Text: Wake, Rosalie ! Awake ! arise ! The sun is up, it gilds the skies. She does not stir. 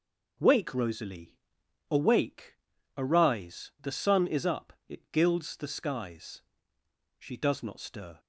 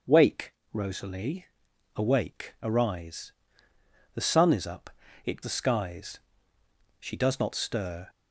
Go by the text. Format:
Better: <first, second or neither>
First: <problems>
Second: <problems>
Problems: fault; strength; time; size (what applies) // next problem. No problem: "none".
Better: first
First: none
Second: skips "gilds"; at 5.4 s